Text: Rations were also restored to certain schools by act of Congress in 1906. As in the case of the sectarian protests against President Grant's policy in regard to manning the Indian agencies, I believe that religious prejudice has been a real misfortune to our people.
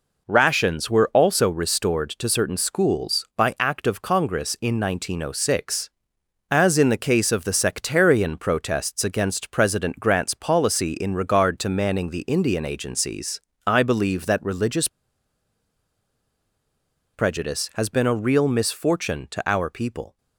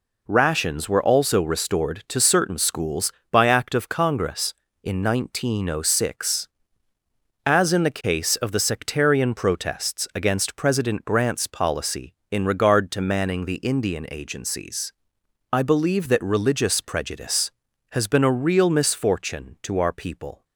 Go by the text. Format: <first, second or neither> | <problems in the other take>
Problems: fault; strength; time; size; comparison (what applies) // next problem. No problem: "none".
second | pauses between "religious" and "prejudice"; strong; at 14.8 s; 2.2 s long